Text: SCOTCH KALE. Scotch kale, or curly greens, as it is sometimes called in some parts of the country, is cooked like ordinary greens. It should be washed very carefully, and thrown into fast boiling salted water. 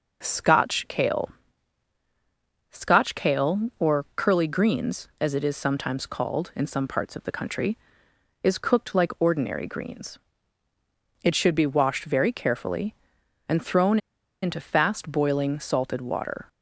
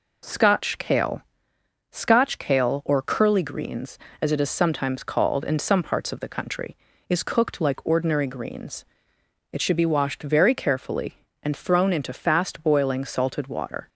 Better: second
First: pauses between "thrown" and "into"; at 13.9 s; 0.45 s long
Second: none

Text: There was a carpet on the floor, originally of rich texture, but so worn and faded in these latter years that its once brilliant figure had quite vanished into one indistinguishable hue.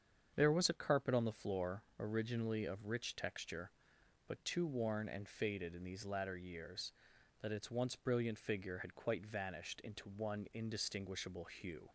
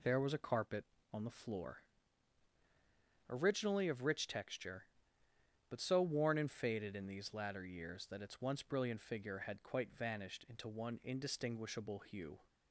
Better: second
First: starts louder than the rest; strong; until 1.3 s; 7.5 dB // says "too" for "so"; at 4.4 s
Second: none

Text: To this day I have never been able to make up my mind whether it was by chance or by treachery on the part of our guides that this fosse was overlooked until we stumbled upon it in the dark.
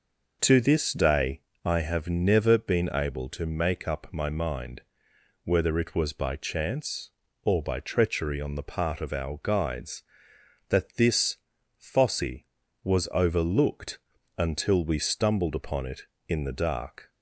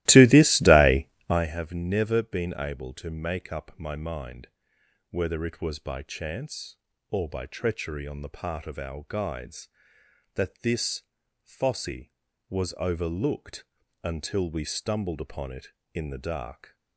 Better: first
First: pauses between "day" and "I"; slight; at 1.4 s; 0.24 s long // pauses between "mind" and "whether"; noticeable; at 4.8 s; 0.62 s long // pauses between "this" and "fosse"; at 11.3 s; 0.42 s long // pauses between "overlooked" and "until"; at 13.9 s; 0.40 s long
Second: starts louder than the rest; strong; until 1.5 s; 16.5 dB // pauses between "day" and "I"; slight; at 1.0 s; 0.22 s long // pauses between "mind" and "whether"; noticeable; at 4.4 s; 0.62 s long // pauses between "this" and "fosse"; at 11.0 s; 0.42 s long // pauses between "overlooked" and "until"; at 13.6 s; 0.40 s long

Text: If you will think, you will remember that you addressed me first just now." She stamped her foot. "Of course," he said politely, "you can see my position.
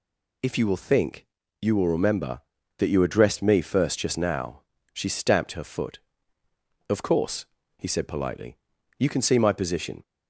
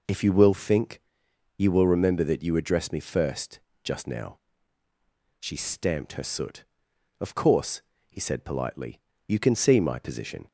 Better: first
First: none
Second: pauses between "first" and "just"; slight; at 3.5 s; 0.24 s long // says "soot" for "foot"; at 6.2 s

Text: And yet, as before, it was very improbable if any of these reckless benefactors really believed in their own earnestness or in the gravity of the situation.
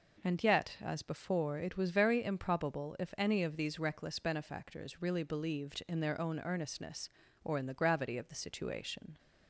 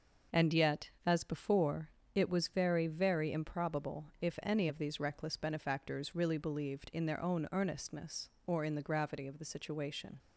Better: first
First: none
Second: says "very" twice; at 2.8 s

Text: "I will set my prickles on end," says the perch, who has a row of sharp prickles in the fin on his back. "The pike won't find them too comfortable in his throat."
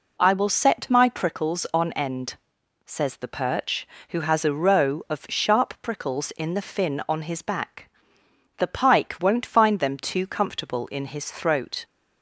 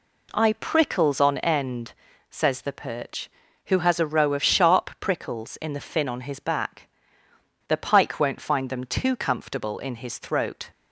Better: first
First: none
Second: skips "will set my"; at 0.5 s

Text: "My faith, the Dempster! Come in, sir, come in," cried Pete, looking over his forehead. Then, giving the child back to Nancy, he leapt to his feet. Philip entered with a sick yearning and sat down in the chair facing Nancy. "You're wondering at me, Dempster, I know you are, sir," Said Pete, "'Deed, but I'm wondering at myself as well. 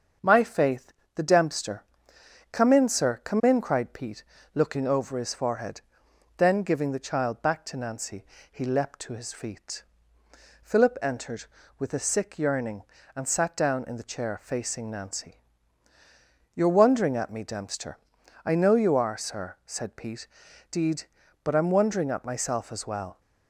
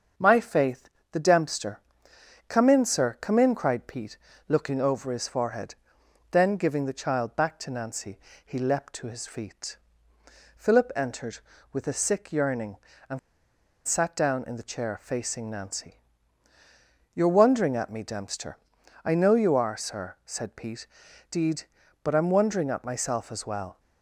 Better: first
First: starts louder than the rest; until 1.4 s; 7 dB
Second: starts louder than the rest; until 1.3 s; 7 dB // pauses between "and" and "sat"; noticeable; at 13.1 s; 0.66 s long

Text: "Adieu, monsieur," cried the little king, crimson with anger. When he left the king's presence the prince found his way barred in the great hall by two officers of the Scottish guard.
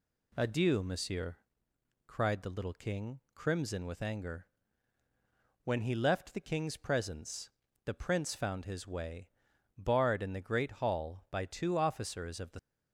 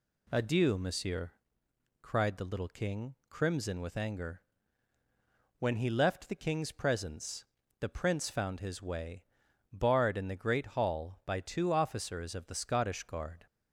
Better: second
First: pauses between "presence" and "the"; slight; at 7.4 s; 0.36 s long // pauses between "way" and "barred"; noticeable; at 9.2 s; 0.48 s long // stops before "Scottish guard"; at 12.5 s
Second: pauses between "presence" and "the"; slight; at 7.4 s; 0.36 s long // pauses between "way" and "barred"; noticeable; at 9.2 s; 0.48 s long

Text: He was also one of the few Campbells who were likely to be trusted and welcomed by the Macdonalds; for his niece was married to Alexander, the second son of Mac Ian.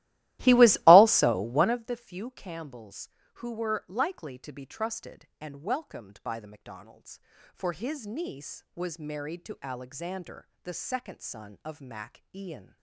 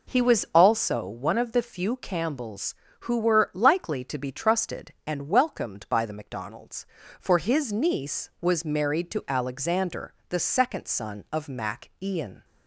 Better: second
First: starts louder than the rest; strong; until 1.9 s; 16.5 dB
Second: none

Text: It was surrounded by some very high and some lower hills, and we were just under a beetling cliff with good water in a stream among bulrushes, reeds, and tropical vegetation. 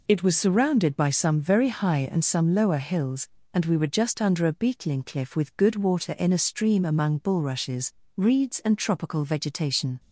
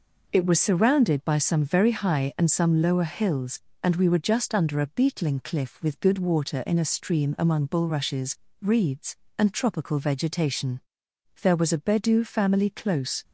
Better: first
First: none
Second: goes on to say "There was a Bedou family close"; strong; from 11.4 s on; 1.8 s long

